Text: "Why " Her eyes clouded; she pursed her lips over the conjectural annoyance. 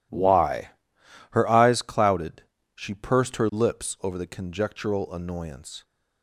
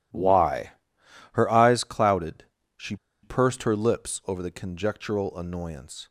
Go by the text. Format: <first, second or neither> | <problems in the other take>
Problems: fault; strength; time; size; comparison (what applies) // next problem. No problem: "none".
first | starts louder than the rest; strong; until 1.4 s; 10 dB; strong in the first // pauses between "she" and "pursed"; slight; at 2.9 s; 0.27 s long